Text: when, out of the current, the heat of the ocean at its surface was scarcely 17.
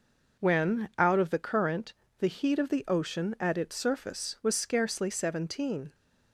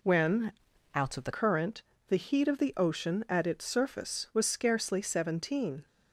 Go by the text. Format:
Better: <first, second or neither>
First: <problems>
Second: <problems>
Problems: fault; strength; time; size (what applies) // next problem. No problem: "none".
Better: first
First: none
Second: changes voice from "out" to "the"; from 0.9 to 1.3 s; 0.4 s long